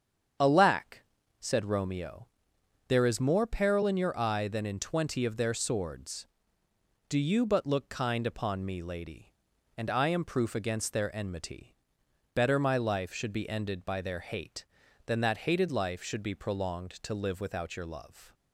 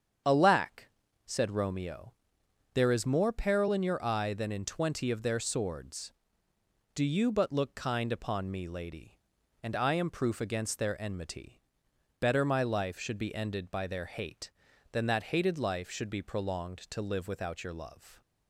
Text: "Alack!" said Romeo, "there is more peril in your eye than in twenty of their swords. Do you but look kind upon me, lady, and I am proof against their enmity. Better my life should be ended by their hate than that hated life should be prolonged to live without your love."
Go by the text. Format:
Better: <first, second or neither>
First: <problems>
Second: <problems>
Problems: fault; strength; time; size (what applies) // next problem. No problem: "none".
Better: neither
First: starts louder than the rest; strong; until 1.7 s; 8 dB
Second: starts louder than the rest; strong; until 1.6 s; 8 dB